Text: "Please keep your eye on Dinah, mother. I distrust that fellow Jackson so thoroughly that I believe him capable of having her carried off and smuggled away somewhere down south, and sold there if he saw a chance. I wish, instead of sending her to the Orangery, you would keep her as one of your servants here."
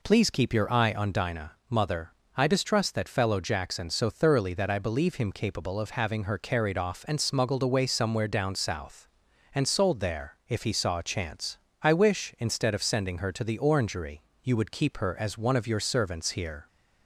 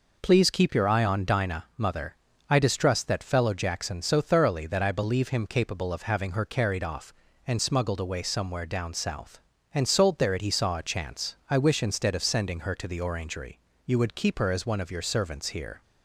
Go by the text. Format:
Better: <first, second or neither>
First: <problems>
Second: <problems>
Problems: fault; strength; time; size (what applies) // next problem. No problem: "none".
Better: first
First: none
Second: says "it" for "if"; at 10.3 s